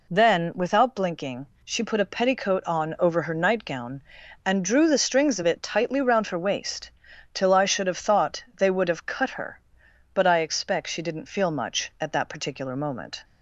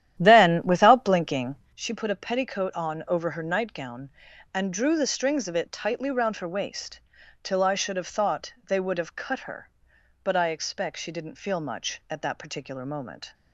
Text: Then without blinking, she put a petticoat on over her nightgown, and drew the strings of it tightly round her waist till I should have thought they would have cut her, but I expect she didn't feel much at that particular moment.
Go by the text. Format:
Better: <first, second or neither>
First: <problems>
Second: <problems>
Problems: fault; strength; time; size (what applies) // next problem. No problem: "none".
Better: first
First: pauses between "waist" and "till"; at 6.9 s; 0.42 s long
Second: starts louder than the rest; strong; until 1.8 s; 11 dB // pauses between "waist" and "till"; at 7.0 s; 0.42 s long